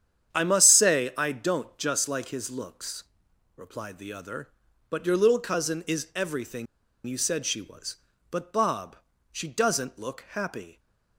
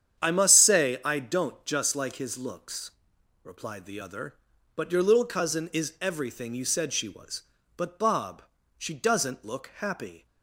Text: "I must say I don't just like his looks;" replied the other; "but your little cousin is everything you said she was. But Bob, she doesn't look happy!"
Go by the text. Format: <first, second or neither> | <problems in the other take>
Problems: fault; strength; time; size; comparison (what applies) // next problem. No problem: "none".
second | starts louder than the rest; strong; until 1.3 s; 8.5 dB; strong in the second // pauses between "everything" and "you"; at 6.6 s; 0.41 s long